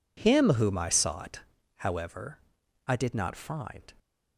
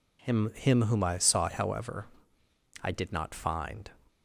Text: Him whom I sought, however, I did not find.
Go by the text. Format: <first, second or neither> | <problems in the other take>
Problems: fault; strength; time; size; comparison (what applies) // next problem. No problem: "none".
first | says "Him" twice; at 0.5 s